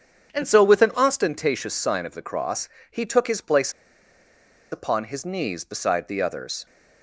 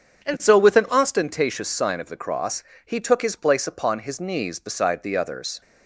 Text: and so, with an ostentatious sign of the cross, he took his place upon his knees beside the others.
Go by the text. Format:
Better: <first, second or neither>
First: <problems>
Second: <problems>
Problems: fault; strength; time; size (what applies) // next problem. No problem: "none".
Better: second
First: starts louder than the rest; strong; until 1.3 s; 8.5 dB // pauses between "place" and "upon"; at 3.7 s; 1.0 s long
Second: starts louder than the rest; strong; until 1.3 s; 8.5 dB